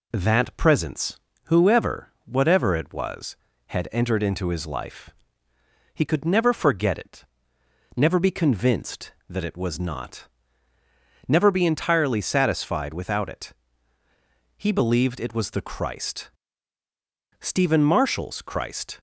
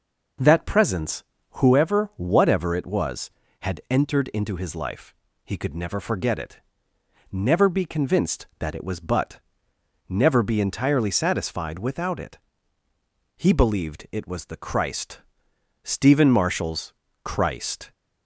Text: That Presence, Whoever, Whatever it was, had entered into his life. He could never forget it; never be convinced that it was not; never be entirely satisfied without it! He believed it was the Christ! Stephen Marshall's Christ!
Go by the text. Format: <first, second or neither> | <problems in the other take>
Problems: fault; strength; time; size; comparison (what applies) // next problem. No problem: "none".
first | says "but" for "not"; at 9.0 s // pauses between "Marshall's" and "Christ"; slight; at 16.9 s; 0.32 s long